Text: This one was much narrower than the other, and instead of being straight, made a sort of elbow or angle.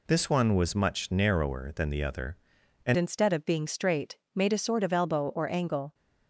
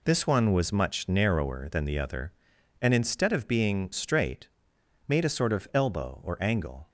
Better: second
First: changes voice at "instead"; from 2.9 s on; 3.0 s long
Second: none

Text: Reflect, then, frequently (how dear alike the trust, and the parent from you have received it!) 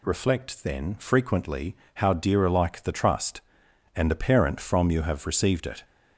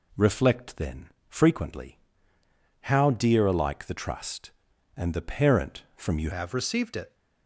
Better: first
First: none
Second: changes voice at "have"; from 6.3 s on; 0.8 s long

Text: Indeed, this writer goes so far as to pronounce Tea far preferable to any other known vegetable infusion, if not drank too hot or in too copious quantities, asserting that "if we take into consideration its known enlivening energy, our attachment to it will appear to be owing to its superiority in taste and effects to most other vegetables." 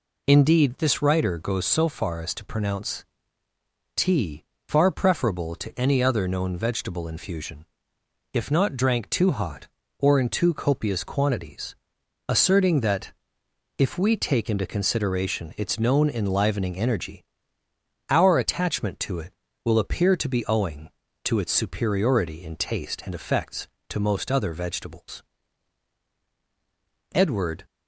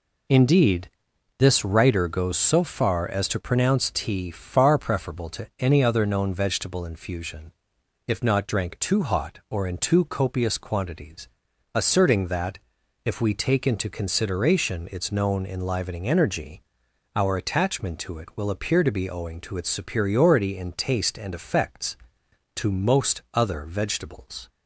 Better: second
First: pauses between "pronounce" and "Tea"; noticeable; at 3.0 s; 0.92 s long // pauses between "Tea" and "far"; slight; at 4.4 s; 0.22 s long // pauses between "that" and "if"; noticeable; at 13.1 s; 0.64 s long // goes on to say "Edward"; from 27.1 s on; 0.50 s long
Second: pauses between "that" and "if"; noticeable; at 12.5 s; 0.46 s long

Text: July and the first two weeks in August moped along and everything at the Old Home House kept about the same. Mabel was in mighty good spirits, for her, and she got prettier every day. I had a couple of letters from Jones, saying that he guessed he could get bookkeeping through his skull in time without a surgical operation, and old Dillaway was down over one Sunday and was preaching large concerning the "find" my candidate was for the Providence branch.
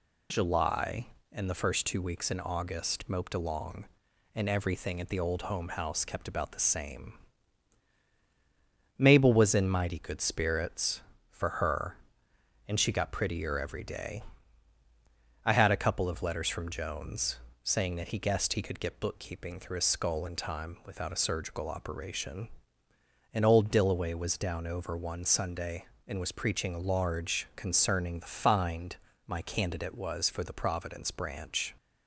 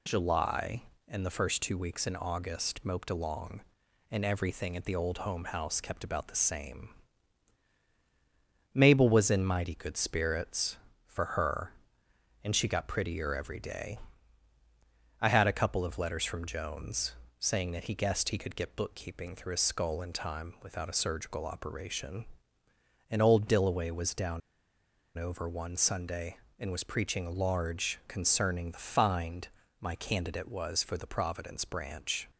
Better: first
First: pauses between "find" and "my"; slight; at 28.9 s; 0.32 s long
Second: pauses between "down" and "over"; noticeable; at 24.4 s; 0.75 s long // pauses between "find" and "my"; slight; at 29.4 s; 0.34 s long

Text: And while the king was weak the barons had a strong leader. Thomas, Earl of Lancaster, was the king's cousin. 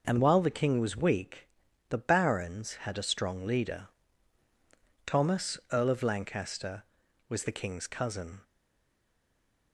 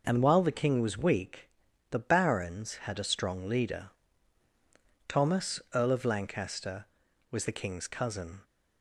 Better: second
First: pauses between "weak" and "the"; at 1.4 s; 0.42 s long // stays silent after the last word; noticeable; from 8.4 s on; 1.3 s long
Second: pauses between "weak" and "the"; at 1.4 s; 0.42 s long

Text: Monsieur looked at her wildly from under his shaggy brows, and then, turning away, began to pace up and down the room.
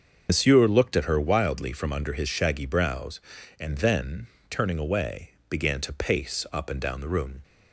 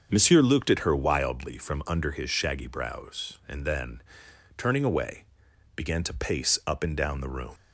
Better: second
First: loses the start of "Monsieur"; at 0.2 s; 80 ms // starts louder than the rest; until 1.3 s; 6.5 dB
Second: starts louder than the rest; until 1.1 s; 6.5 dB

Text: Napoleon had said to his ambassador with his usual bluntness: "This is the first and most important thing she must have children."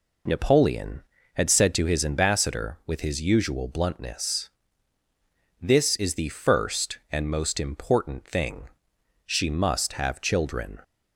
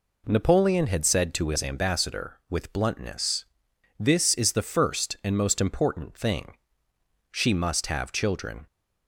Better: first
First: pauses between "thing" and "she"; noticeable; at 8.6 s; 0.58 s long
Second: skips "his usual"; at 2.7 s // pauses between "thing" and "she"; noticeable; at 6.5 s; 0.76 s long

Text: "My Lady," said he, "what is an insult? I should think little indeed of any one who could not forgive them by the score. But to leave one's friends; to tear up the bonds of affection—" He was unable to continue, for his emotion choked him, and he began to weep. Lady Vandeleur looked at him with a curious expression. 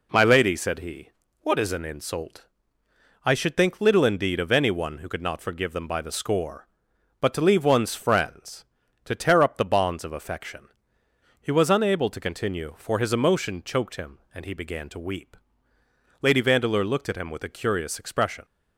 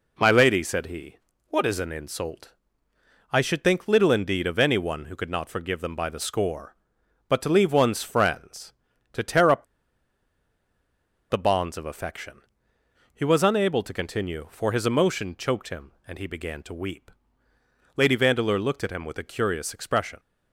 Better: first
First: none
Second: pauses between "up" and "the"; strong; at 9.6 s; 1.6 s long

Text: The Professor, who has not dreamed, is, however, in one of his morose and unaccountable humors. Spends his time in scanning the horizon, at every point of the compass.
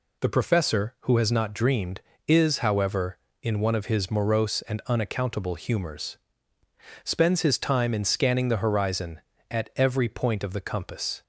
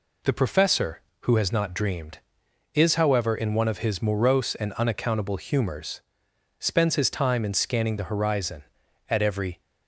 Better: first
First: none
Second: stops before "point of the compass"; at 9.6 s

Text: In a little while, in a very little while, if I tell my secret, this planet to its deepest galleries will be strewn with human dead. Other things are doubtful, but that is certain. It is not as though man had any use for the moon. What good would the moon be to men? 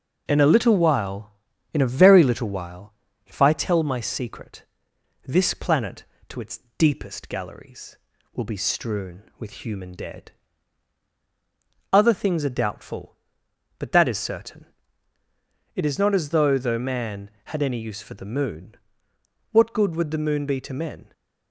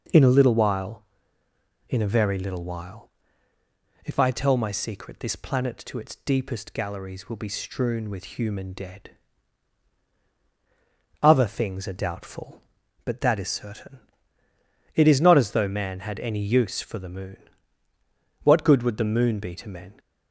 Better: second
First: pauses between "its" and "deepest"; slight; at 6.5 s; 0.20 s long // says "though" twice; at 16.5 s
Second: none

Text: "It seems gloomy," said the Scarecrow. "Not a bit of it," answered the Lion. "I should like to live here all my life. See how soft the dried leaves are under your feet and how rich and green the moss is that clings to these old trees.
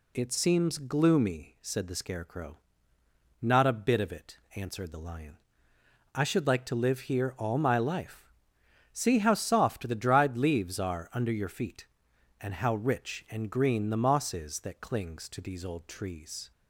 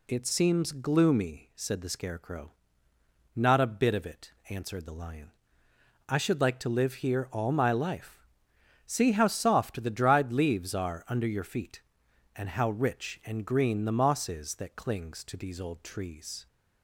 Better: neither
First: none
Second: none

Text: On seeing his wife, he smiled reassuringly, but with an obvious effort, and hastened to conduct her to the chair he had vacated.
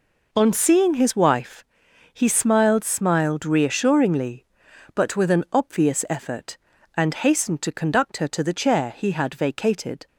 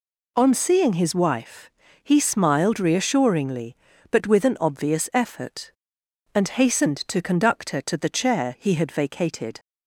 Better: second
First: says "smiled" twice; at 2.8 s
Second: none

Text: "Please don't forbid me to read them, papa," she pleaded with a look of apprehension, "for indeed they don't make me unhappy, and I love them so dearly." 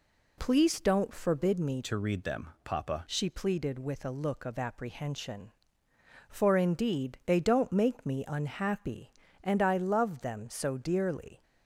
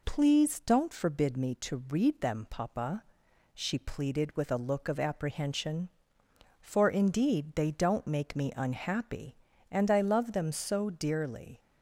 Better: second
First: changes voice from "to" to "papa"; from 1.8 to 3.0 s; 1.2 s long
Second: none

